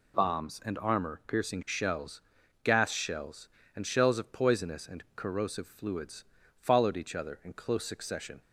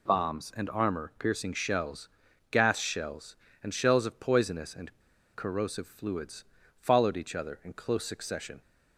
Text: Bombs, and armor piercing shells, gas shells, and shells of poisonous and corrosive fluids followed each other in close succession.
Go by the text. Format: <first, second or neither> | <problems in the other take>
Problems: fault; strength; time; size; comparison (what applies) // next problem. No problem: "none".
first | pauses between "and" and "corrosive"; at 4.9 s; 0.44 s long // pauses between "fluids" and "followed"; slight; at 6.4 s; 0.34 s long; slight in the first